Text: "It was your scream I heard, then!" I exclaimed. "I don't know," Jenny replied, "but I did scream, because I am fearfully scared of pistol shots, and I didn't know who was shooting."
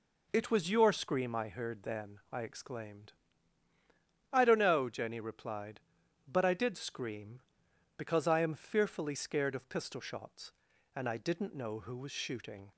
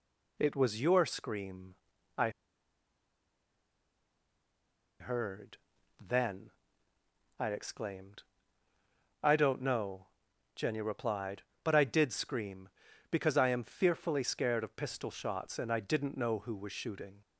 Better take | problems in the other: first | pauses between "scream" and "I"; at 1.7 s; 0.42 s long // pauses between "I" and "heard"; strong; at 2.2 s; 2.7 s long

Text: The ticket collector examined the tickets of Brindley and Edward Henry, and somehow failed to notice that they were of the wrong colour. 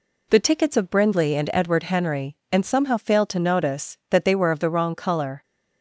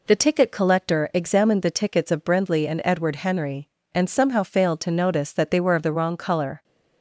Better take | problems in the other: second | skips "ticket collector examined the"; at 0.4 s

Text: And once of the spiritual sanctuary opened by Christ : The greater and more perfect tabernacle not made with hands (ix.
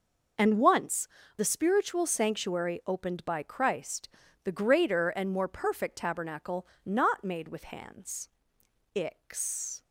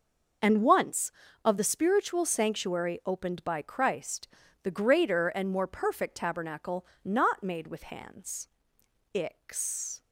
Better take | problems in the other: second | skips "of"; at 1.2 s // pauses between "tabernacle" and "not"; slight; at 6.6 s; 0.20 s long; slight in the second

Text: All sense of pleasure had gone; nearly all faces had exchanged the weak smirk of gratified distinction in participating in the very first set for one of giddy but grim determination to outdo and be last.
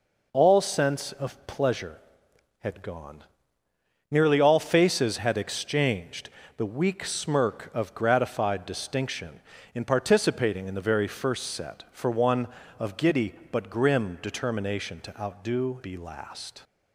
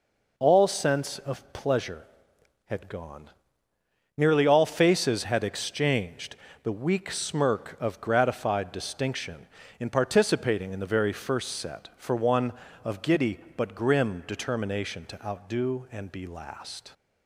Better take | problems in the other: second | pauses between "exchanged" and "the"; slight; at 6.2 s; 0.30 s long; slight in the second // skips "and"; at 15.8 s

